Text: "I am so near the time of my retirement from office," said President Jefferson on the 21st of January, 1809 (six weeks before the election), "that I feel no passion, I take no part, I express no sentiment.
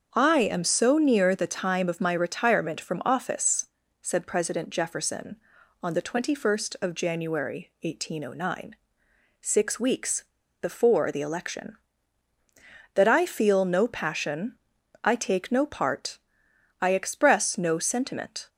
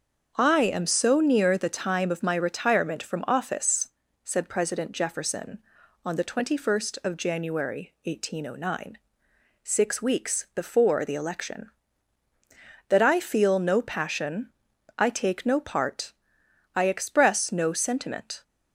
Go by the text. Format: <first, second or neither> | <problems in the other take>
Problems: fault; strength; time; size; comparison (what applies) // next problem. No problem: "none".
second | starts louder than the rest; until 1.1 s; 7 dB; also in the second // pauses between "weeks" and "before"; at 10.2 s; 0.36 s long